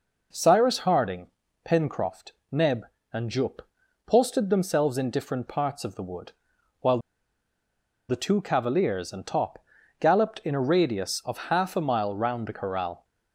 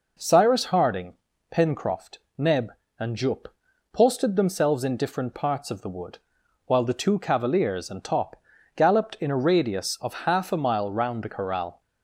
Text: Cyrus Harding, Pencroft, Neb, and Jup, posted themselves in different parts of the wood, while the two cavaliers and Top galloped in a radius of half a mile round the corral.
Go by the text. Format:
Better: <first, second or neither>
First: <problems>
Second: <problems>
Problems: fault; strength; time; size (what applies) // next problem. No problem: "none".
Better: second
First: pauses between "while" and "the"; at 6.9 s; 1.1 s long // pauses between "Top" and "galloped"; at 9.6 s; 0.38 s long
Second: pauses between "Top" and "galloped"; at 8.3 s; 0.36 s long